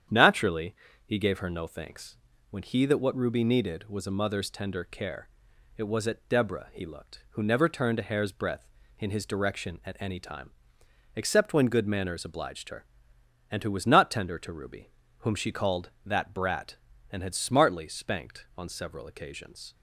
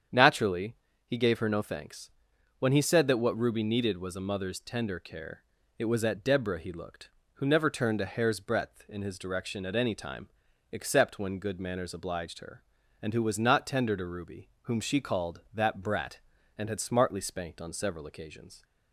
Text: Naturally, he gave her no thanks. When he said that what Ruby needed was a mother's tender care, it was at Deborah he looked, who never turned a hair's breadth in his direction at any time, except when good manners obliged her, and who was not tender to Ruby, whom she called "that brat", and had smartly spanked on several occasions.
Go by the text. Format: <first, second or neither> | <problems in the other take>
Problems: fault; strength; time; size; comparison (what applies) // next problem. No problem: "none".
second | starts louder than the rest; strong; until 1.3 s; 9 dB; strong in the second // skips "said"; at 2.8 s